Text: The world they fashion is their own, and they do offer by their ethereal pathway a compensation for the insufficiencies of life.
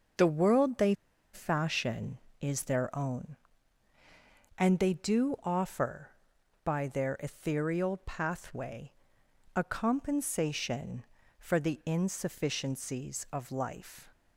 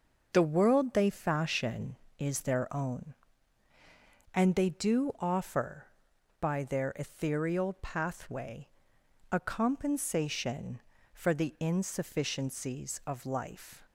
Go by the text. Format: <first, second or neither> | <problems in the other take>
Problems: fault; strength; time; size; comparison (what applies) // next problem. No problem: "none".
second | pauses between "they" and "fashion"; at 0.9 s; 0.39 s long // pauses between "pathway" and "a"; noticeable; at 8.9 s; 0.64 s long; noticeable in the second